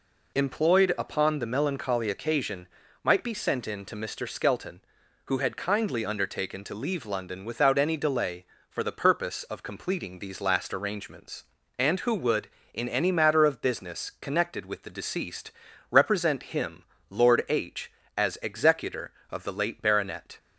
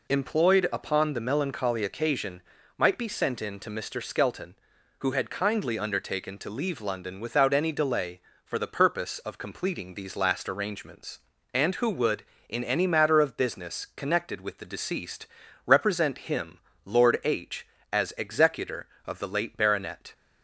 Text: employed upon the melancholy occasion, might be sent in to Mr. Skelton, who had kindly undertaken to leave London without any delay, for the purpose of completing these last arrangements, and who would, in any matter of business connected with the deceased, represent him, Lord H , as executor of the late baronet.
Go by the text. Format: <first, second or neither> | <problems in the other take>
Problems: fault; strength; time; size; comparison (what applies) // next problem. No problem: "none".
neither | none